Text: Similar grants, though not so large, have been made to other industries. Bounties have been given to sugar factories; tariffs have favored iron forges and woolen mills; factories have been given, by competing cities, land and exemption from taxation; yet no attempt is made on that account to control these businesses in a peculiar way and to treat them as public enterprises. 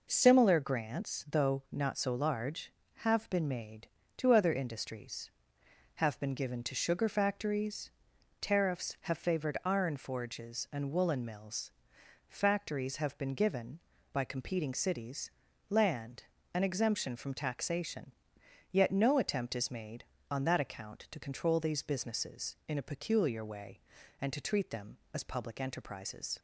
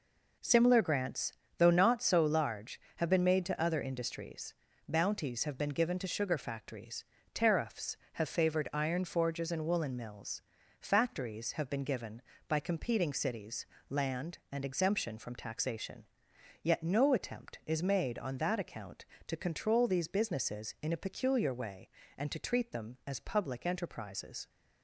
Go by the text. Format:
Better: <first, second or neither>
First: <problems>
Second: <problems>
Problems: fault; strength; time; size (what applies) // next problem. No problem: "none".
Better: second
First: skips "Bounties"; at 5.6 s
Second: none